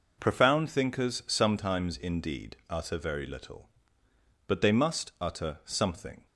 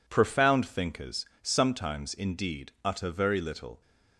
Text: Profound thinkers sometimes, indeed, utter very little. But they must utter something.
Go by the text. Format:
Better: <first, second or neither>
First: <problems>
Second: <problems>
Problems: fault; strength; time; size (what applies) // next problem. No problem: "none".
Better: first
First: none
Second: pauses between "thinkers" and "sometimes"; slight; at 1.2 s; 0.18 s long // stops before "But they must utter something"; at 3.8 s